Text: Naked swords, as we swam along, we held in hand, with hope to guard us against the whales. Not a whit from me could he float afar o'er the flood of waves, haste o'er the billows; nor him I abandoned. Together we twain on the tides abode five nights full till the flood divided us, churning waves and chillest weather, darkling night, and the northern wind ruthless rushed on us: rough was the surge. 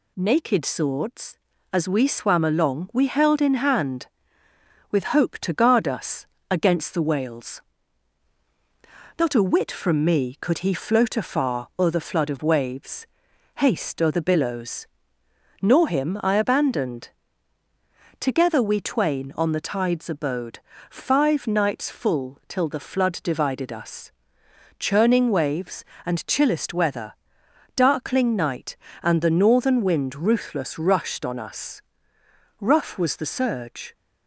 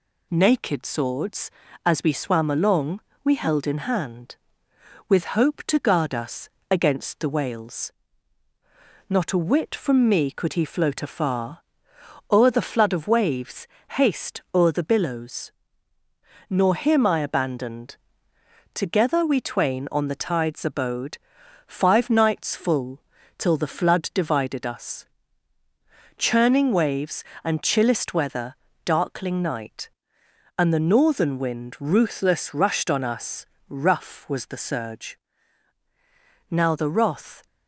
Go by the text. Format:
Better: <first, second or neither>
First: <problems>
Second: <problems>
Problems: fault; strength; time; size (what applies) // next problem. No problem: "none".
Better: first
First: pauses between "us" and "against"; slight; at 6.2 s; 0.24 s long // pauses between "abode" and "five"; slight; at 20.5 s; 0.30 s long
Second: pauses between "us" and "against"; slight; at 6.5 s; 0.20 s long // pauses between "afar" and "o'er"; noticeable; at 11.5 s; 0.70 s long // pauses between "abode" and "five"; noticeable; at 21.1 s; 0.48 s long // pauses between "full" and "till"; slight; at 23.0 s; 0.36 s long // goes on to say "Now the wrath"; noticeable; from 36.4 s on; 0.96 s long